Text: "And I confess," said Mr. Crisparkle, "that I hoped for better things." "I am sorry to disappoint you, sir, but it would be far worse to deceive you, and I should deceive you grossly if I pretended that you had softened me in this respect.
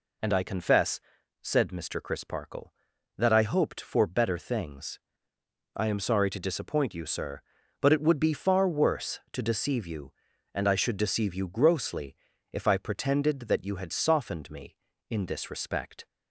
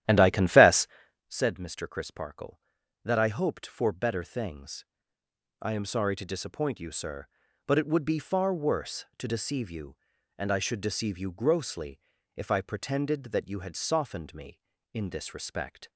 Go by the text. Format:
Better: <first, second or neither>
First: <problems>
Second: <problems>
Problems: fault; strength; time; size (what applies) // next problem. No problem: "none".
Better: first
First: pauses between "grossly" and "if"; slight; at 12.1 s; 0.34 s long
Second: starts louder than the rest; strong; until 1.3 s; 12 dB // pauses between "grossly" and "if"; slight; at 11.9 s; 0.34 s long